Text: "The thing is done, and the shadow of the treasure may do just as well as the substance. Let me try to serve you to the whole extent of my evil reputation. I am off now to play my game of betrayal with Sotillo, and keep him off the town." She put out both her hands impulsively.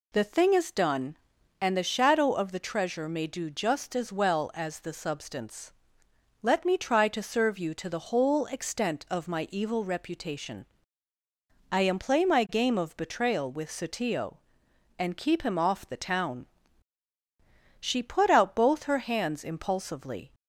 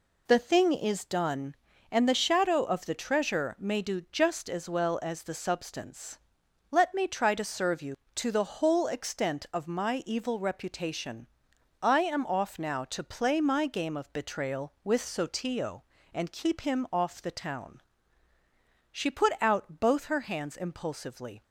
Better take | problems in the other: second | skips "off now to"; at 11.9 s

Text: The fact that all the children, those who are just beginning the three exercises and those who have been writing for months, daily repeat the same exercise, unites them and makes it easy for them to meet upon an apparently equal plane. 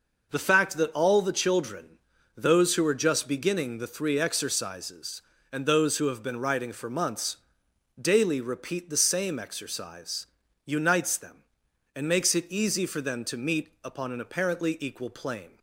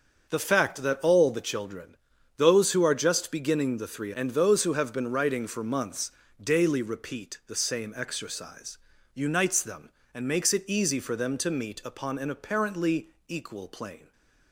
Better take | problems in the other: first | starts louder than the rest; until 1.3 s; 6.5 dB // skips "exercises"; at 4.1 s // pauses between "apparently" and "equal"; slight; at 13.0 s; 0.20 s long

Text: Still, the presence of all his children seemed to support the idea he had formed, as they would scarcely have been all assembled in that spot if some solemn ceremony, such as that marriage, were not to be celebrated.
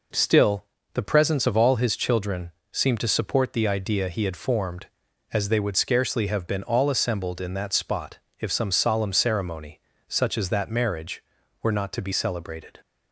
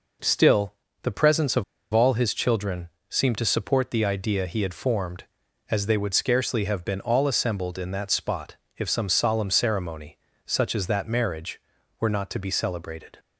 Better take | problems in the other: first | pauses between "of" and "all"; slight; at 1.6 s; 0.30 s long // pauses between "children" and "seemed"; slight; at 2.8 s; 0.22 s long; slight in the first // pauses between "spot" and "if"; slight; at 8.5 s; 0.22 s long; slight in the first

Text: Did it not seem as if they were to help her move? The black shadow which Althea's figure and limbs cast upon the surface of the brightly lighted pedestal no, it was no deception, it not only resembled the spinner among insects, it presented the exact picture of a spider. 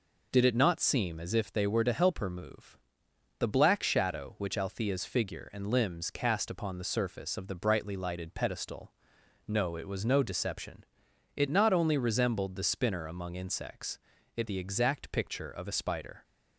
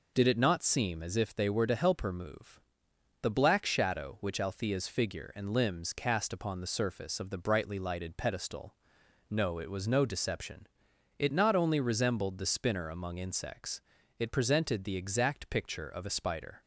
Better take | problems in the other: second | pauses between "pedestal" and "no"; noticeable; at 8.9 s; 0.56 s long; noticeable in the second // skips "presented"; at 14.4 s

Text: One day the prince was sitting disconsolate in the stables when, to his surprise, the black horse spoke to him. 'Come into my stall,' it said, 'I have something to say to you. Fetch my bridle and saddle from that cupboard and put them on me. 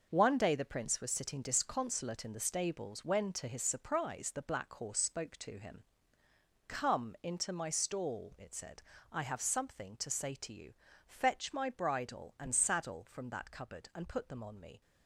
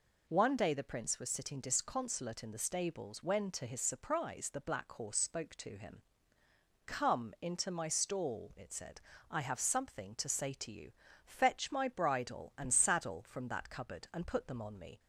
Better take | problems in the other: second | gets quieter; strong; throughout; 8.5 dB

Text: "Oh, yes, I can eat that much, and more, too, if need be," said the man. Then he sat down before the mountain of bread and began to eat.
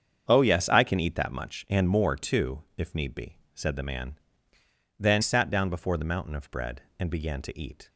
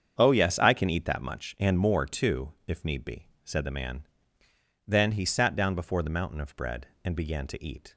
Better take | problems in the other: second | starts louder than the rest; strong; until 1.2 s; 7.5 dB; strong in the second // skips "he"; at 5.2 s

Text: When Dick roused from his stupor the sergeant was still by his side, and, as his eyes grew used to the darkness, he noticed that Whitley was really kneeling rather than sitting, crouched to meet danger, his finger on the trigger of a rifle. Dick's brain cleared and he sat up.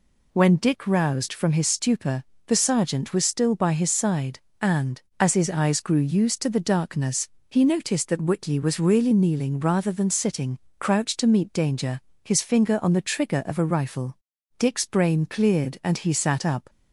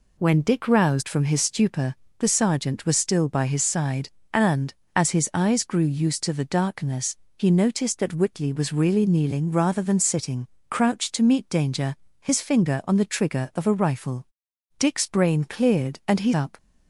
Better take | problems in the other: first | pauses between "stupor" and "the"; slight; at 1.9 s; 0.24 s long; slight in the first // skips "sat"; at 16.3 s

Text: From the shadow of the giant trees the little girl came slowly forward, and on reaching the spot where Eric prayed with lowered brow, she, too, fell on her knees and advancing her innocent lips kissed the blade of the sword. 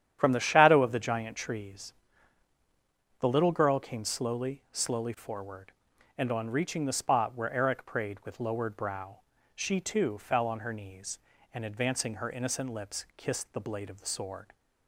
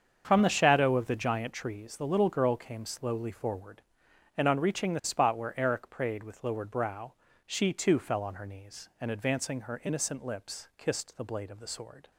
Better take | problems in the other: second | starts louder than the rest; strong; until 1.2 s; 10 dB; strong in the second // pauses between "trees" and "the"; strong; at 1.9 s; 1.2 s long // says "slowly" twice; at 4.6 s

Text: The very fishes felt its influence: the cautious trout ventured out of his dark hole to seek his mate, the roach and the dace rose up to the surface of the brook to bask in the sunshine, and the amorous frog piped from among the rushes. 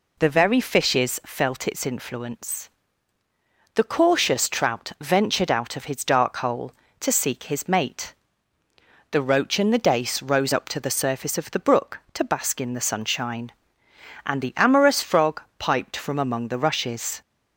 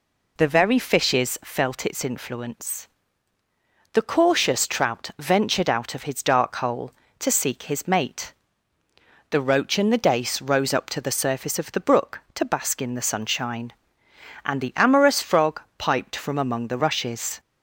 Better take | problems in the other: neither | pauses between "frog" and "piped"; slight; the same in both

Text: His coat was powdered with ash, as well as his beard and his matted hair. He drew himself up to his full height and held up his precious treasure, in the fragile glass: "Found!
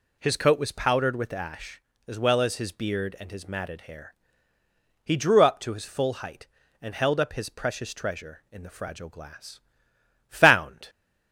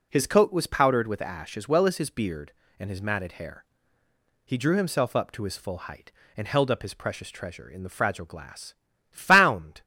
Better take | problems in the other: second | skips "himself"; at 5.4 s

